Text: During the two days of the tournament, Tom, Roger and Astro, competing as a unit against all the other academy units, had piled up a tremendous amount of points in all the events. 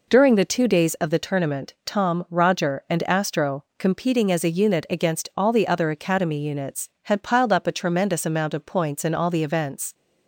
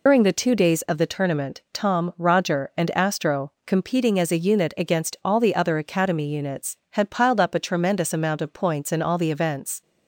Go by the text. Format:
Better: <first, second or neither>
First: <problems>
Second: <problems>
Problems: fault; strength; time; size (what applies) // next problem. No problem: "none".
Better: first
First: none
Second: loses the start of "During"; at 0.0 s; 80 ms